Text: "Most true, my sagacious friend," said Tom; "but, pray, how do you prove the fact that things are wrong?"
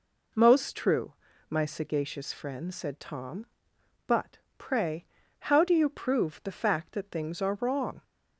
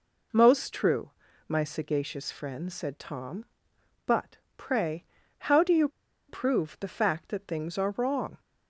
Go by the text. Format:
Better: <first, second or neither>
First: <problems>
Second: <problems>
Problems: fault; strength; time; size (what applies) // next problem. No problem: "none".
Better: first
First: none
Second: pauses between "you" and "prove"; at 5.8 s; 0.40 s long